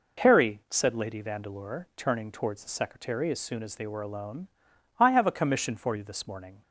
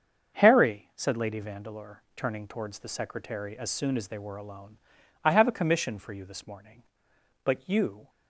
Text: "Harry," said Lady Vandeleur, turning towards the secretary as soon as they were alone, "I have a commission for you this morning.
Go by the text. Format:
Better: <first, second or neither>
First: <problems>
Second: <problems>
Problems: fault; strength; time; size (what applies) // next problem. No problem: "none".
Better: first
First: none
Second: starts louder than the rest; until 1.4 s; 6.5 dB // goes on to say "But you"; noticeable; from 7.4 s on; 0.64 s long